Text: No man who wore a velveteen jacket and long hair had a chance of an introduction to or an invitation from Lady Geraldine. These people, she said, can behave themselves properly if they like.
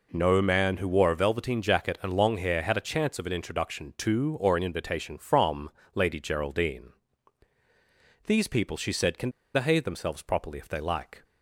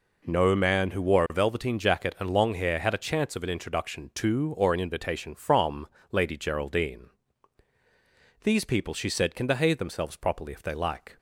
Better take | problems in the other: second | pauses between "from" and "Lady"; slight; at 5.6 s; 0.24 s long; slight in the second // pauses between "can" and "behave"; slight; at 9.2 s; 0.25 s long

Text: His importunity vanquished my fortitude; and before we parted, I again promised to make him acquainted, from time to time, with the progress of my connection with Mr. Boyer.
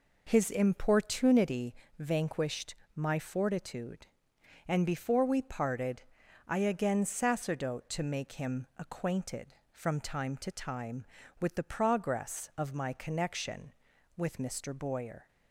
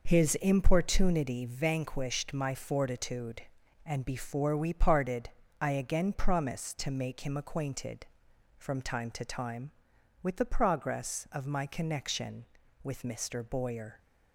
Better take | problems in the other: second | pauses between "importunity" and "vanquished"; slight; at 1.7 s; 0.24 s long // pauses between "vanquished" and "my"; slight; at 2.7 s; 0.18 s long // says "sacerdote" for "promised"; at 7.0 s

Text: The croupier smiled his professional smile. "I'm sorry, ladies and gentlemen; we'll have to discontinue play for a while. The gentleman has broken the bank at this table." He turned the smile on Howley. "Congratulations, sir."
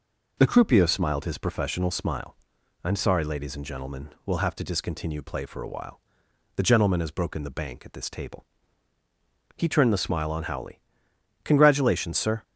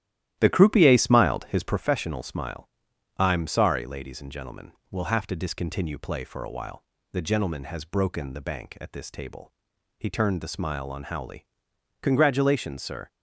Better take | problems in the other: first | starts louder than the rest; strong; until 1.8 s; 13 dB

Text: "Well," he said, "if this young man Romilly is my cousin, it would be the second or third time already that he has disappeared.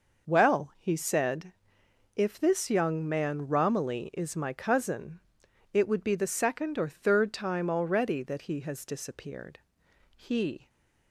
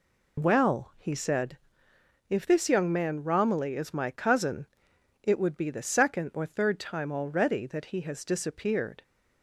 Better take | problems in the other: second | goes on to say "He"; from 10.1 s on; 0.54 s long

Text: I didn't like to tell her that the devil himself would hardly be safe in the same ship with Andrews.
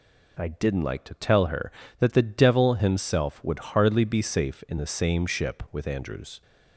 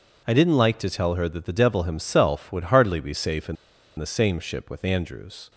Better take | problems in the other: first | pauses between "in" and "the"; at 3.5 s; 0.42 s long

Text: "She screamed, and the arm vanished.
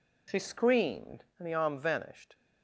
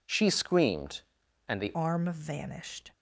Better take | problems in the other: first | changes voice at "arm"; from 1.7 s on; 1.1 s long

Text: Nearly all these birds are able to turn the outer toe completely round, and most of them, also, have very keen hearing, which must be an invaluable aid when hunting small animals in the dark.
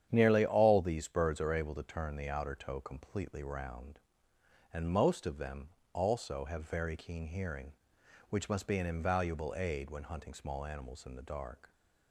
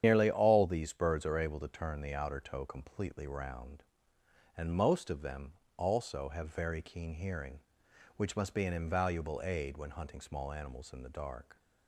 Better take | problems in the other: first | loses the start of "Nearly"; at 0.0 s; 90 ms // starts louder than the rest; strong; until 1.0 s; 9 dB; strong in the first

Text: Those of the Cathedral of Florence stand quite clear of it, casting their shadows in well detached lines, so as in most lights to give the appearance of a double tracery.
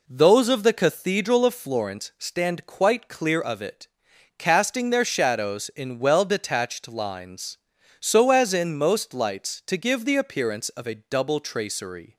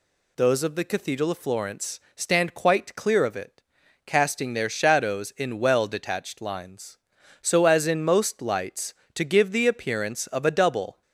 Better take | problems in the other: first | pauses between "Florence" and "stand"; slight; at 1.9 s; 0.17 s long // stops before "tracery"; at 11.0 s

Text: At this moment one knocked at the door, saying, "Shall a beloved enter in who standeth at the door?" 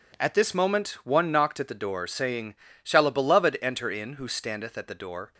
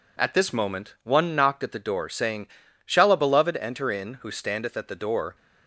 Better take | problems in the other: neither | none

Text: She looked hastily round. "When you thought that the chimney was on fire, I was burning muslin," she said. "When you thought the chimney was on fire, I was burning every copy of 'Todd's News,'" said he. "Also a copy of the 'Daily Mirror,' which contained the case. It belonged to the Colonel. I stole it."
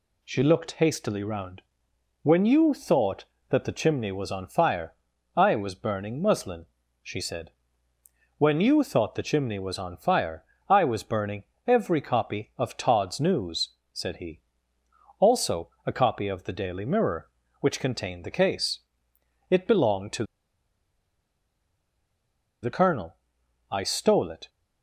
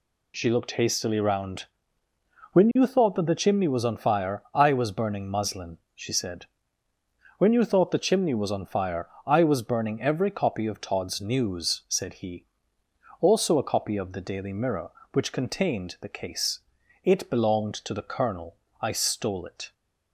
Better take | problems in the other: second | pauses between "burning" and "every"; slight; at 11.4 s; 0.24 s long // pauses between "to" and "the"; strong; at 20.2 s; 2.3 s long

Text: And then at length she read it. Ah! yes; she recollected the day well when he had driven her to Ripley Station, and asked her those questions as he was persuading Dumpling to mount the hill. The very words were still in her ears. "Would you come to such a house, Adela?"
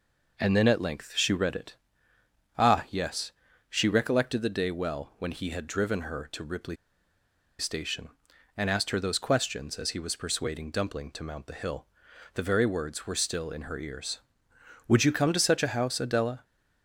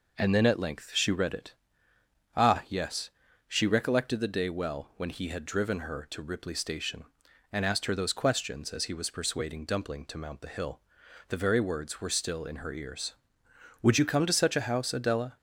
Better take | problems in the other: second | pauses between "Ripley" and "Station"; noticeable; at 6.7 s; 0.83 s long

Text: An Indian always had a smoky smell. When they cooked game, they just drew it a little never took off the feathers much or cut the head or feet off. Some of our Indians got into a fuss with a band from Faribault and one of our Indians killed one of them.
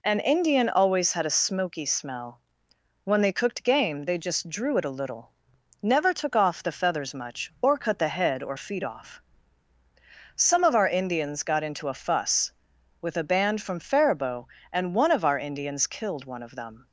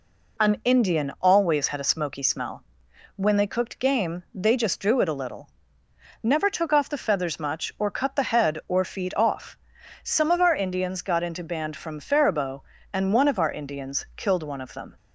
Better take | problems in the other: first | pauses between "little" and "never"; noticeable; at 5.4 s; 0.74 s long; noticeable in the first // skips "a fuss with a"; at 11.4 s

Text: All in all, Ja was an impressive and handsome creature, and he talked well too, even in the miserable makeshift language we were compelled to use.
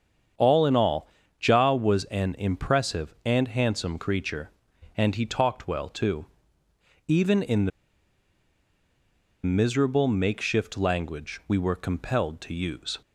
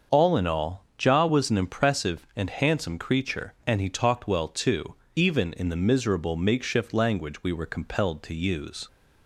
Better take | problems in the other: second | starts louder than the rest; strong; until 1.7 s; 8 dB; also in the second // pauses between "the" and "miserable"; strong; at 7.7 s; 1.7 s long

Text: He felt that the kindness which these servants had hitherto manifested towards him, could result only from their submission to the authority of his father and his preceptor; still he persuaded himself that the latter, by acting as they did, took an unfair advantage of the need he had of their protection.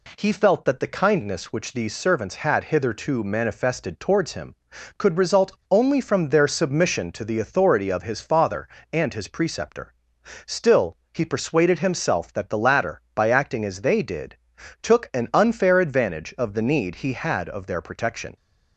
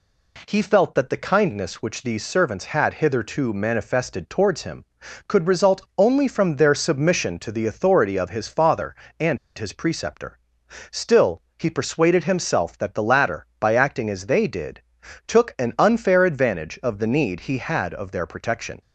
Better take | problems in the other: first | pauses between "result" and "only"; slight; at 5.8 s; 0.16 s long; slight in the first // pauses between "and" and "his"; slight; at 9.3 s; 0.20 s long // pauses between "still" and "he"; slight; at 11.4 s; 0.18 s long; slight in the first

